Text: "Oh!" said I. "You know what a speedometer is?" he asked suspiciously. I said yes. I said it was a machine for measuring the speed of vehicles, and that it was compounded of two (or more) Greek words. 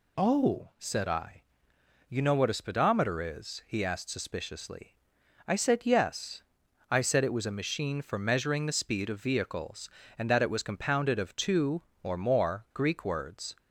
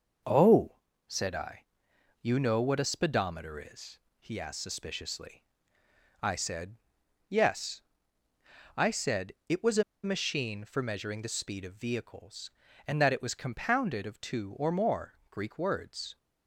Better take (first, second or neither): first